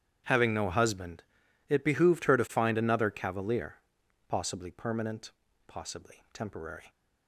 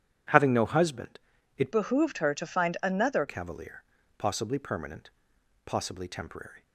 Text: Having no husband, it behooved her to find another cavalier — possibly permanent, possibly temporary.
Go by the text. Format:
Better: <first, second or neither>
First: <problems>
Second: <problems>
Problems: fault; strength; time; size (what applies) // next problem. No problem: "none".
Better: first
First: starts louder than the rest; strong; until 1.7 s; 9.5 dB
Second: starts louder than the rest; strong; until 1.6 s; 10 dB // changes voice from "behooved" to "another"; from 1.7 to 3.2 s; 1.5 s long